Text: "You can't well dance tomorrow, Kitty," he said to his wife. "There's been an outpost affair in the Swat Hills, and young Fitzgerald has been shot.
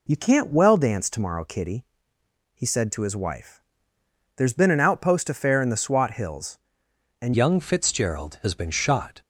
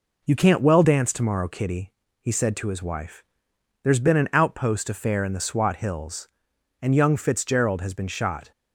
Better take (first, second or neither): second